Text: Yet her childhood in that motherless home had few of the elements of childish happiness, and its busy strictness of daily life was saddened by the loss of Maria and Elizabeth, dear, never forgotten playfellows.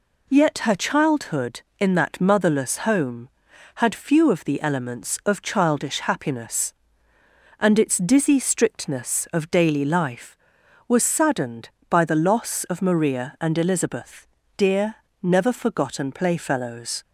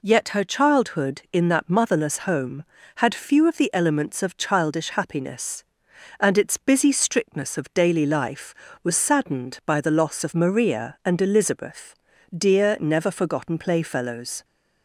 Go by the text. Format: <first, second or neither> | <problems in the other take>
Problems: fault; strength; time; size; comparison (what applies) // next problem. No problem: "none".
second | says "dizzy" for "busy"; at 7.9 s